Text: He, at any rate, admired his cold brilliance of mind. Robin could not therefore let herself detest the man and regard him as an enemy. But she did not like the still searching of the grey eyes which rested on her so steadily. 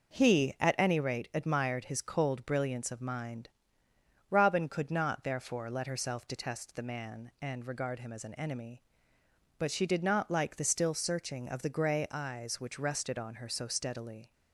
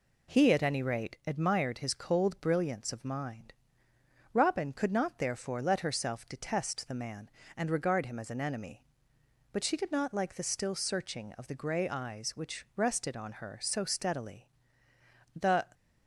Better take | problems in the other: first | goes on to say "The"; slight; from 15.3 s on; 0.30 s long

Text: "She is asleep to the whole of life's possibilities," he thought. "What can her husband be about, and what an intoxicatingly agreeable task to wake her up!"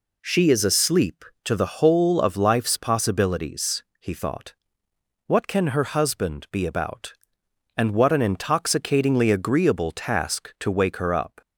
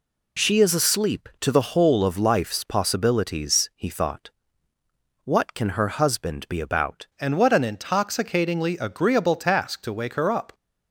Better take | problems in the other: first | changes voice at "and"; from 7.1 s on; 3.4 s long

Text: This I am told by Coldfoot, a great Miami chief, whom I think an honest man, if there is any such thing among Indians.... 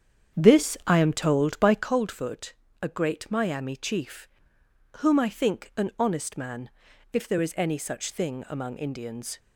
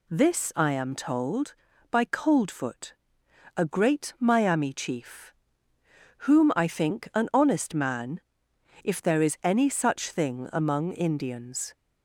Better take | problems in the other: second | starts louder than the rest; strong; until 1.9 s; 8.5 dB

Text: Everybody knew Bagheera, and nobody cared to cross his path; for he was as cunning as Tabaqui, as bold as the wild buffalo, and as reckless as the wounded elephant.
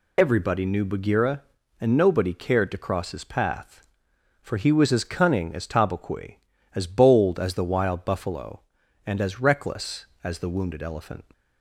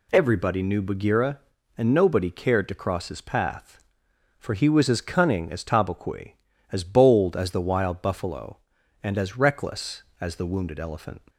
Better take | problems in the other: second | loses the start of "Everybody"; at 0.1 s; 40 ms

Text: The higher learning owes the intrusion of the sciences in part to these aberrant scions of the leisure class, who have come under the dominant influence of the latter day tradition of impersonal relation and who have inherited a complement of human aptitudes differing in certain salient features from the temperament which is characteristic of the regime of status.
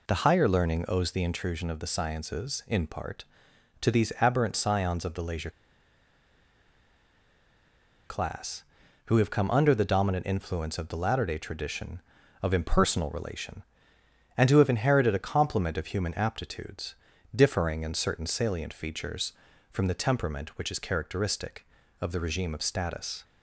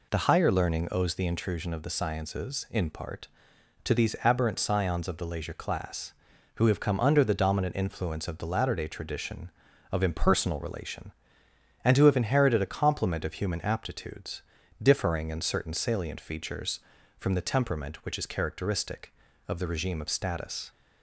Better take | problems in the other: second | pauses between "leisure" and "class"; strong; at 5.4 s; 2.5 s long // pauses between "aptitudes" and "differing"; at 16.9 s; 0.38 s long; also in the second

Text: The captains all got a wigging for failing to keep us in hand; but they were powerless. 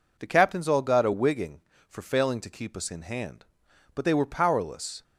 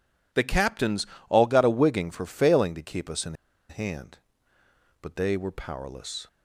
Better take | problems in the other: first | pauses between "captains" and "all"; slight; at 1.0 s; 0.22 s long // pauses between "in" and "hand"; slight; at 3.3 s; 0.35 s long

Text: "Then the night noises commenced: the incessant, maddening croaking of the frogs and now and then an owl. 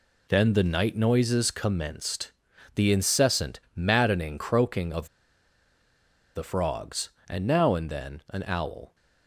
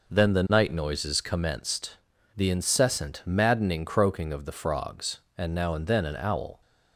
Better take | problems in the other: second | pauses between "of" and "the"; strong; at 5.0 s; 1.2 s long

